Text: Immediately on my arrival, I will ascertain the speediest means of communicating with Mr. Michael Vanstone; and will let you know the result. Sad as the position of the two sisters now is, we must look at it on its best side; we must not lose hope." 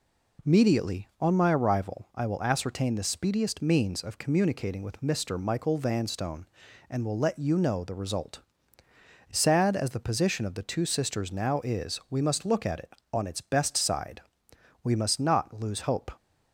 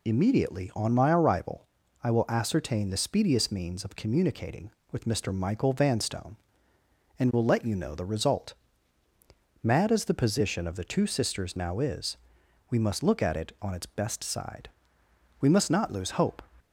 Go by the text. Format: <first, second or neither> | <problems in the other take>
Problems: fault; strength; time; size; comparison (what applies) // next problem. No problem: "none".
first | says "Mad" for "Sad"; at 9.6 s